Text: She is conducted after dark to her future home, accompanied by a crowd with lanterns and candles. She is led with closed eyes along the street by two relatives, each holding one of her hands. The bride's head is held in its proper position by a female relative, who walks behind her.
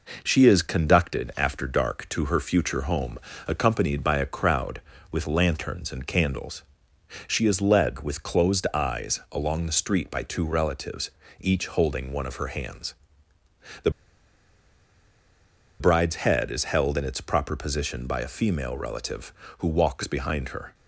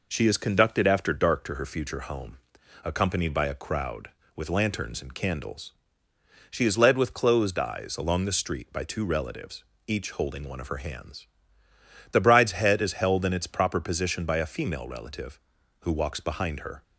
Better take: second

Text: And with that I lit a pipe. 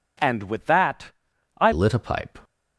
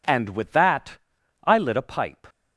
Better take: second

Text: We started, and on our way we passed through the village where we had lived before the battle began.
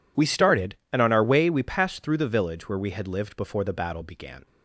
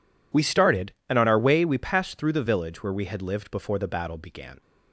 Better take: neither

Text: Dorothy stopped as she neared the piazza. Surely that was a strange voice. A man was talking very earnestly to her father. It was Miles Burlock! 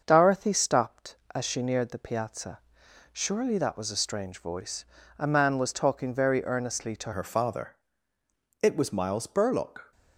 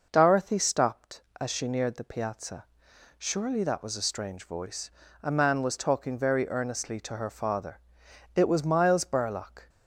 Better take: second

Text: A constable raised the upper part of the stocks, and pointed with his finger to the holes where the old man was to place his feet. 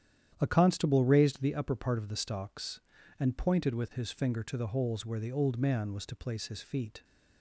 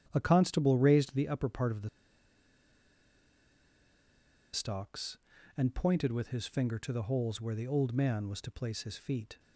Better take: first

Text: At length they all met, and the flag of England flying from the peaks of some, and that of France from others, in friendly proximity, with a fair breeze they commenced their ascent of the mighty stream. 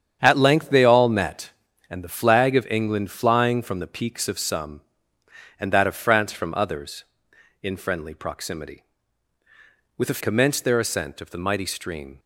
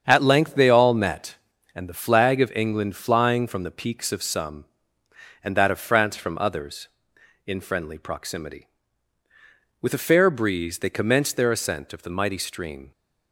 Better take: second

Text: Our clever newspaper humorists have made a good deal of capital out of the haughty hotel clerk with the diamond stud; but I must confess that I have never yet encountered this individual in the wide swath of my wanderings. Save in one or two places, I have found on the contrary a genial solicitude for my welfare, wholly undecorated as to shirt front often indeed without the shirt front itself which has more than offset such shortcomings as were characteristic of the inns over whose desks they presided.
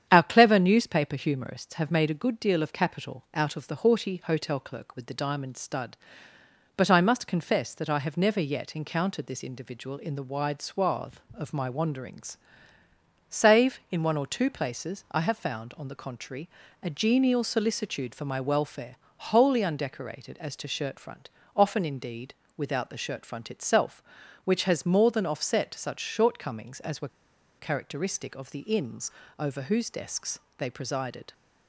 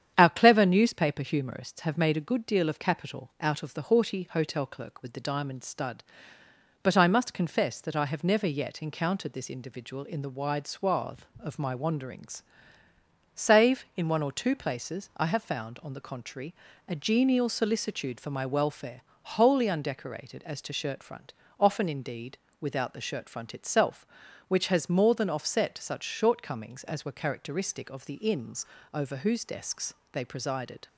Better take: second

